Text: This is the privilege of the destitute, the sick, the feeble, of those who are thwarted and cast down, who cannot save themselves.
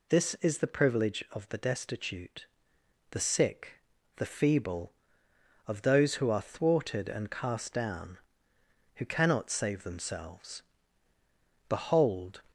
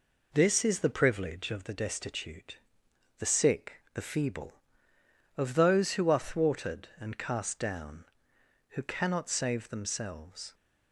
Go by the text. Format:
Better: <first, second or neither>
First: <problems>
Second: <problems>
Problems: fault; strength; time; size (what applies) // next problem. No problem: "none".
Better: second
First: goes on to say "Behold"; noticeable; from 11.7 s on; 0.72 s long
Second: none